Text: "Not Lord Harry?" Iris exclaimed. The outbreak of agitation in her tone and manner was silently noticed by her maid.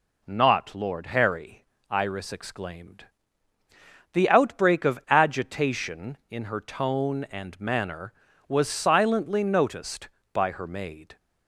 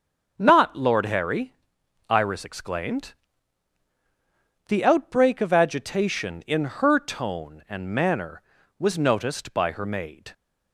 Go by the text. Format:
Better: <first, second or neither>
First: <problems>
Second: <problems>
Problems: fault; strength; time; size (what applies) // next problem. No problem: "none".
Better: first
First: none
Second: starts louder than the rest; until 1.3 s; 6.5 dB // skips "silently"; at 8.9 s